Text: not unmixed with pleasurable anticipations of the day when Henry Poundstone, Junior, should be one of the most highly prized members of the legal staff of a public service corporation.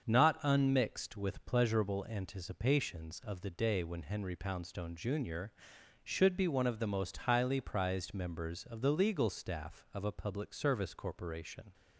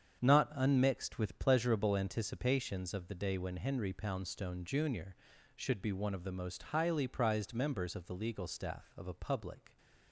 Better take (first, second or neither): first